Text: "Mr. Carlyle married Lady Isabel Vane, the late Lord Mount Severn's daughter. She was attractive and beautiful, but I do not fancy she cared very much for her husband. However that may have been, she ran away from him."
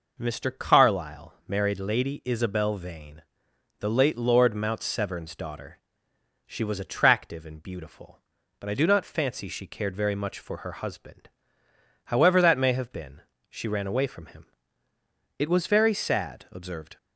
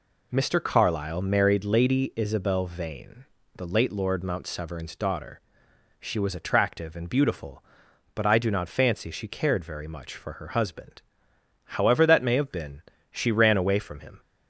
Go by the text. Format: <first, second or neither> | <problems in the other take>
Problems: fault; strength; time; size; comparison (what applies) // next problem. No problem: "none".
second | goes on to say "It was very sad observed"; from 15.3 s on; 1.5 s long